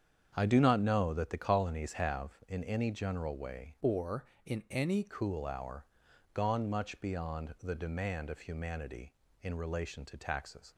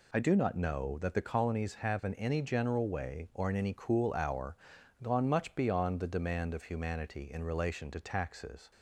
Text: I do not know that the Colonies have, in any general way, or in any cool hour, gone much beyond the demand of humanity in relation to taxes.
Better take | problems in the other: second | starts louder than the rest; strong; until 1.3 s; 8 dB // changes voice from "or" to "any"; from 3.8 to 5.0 s; 1.2 s long

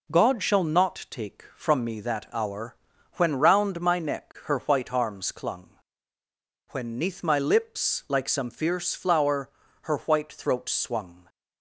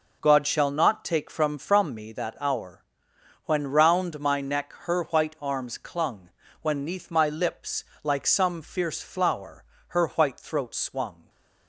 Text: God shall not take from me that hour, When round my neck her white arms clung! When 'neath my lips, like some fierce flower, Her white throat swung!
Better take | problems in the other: first | says "from" twice; at 1.5 s

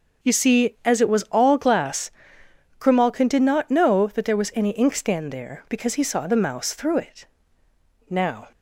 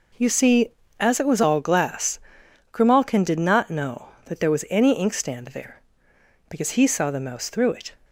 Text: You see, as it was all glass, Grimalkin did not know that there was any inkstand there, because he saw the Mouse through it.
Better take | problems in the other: second | starts louder than the rest; until 1.4 s; 6 dB // goes on to say "Now"; slight; from 8.0 s on; 0.42 s long

